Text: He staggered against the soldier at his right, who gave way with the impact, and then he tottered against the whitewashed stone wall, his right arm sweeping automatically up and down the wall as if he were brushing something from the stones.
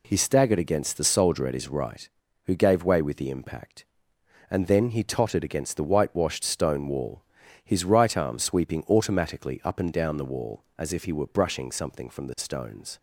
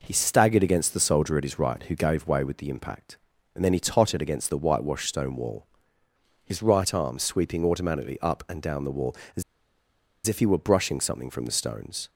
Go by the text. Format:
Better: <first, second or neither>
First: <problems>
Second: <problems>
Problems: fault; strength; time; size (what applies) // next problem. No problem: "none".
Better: first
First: none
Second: pauses between "as" and "if"; noticeable; at 9.4 s; 0.84 s long